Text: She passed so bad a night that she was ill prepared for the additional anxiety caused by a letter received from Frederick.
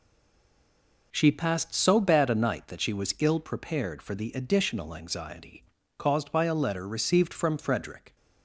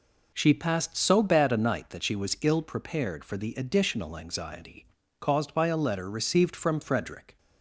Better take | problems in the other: second | stays silent before the first word; until 1.1 s; 1.1 s long // pauses between "anxiety" and "caused"; slight; at 5.6 s; 0.36 s long; slight in the second

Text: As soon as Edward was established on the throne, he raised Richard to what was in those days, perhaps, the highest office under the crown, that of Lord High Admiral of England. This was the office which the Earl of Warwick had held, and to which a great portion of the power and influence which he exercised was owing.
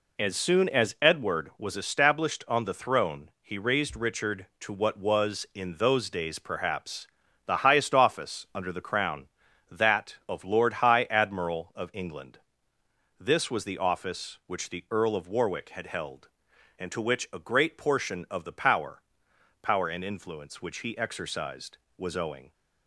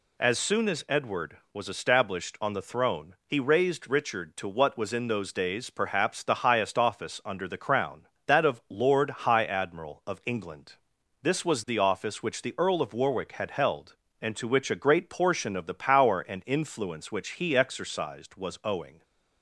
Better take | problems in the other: second | says "power" twice; at 19.6 s

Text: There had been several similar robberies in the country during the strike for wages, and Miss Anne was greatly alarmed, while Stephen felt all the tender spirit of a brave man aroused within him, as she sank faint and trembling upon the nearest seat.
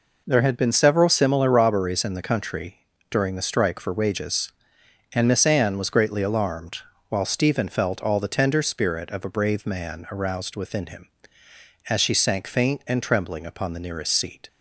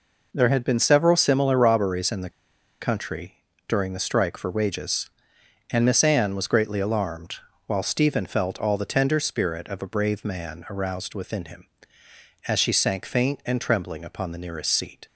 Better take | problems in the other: first | pauses between "the" and "country"; noticeable; at 2.2 s; 0.51 s long // pauses between "country" and "during"; slight; at 3.3 s; 0.30 s long; slight in the first

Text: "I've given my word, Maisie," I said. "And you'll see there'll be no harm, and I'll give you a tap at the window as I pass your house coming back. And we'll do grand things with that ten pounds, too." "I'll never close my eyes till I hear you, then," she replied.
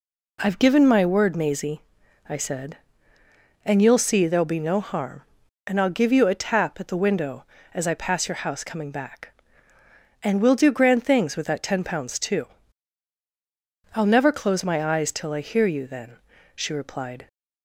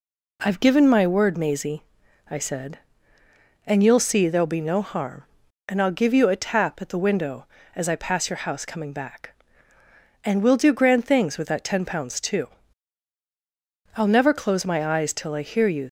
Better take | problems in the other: first | stops before "then she replied"; at 15.8 s

